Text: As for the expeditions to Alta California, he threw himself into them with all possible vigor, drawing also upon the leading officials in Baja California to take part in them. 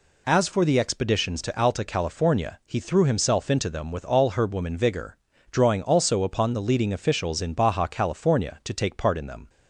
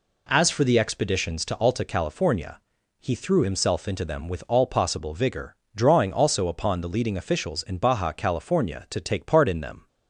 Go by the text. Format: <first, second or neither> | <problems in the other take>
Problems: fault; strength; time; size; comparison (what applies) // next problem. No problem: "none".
second | says "herbwoman" for "possible"; at 4.3 s